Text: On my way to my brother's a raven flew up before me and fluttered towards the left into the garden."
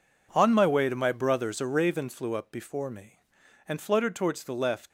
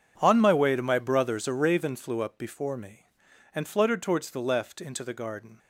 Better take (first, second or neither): second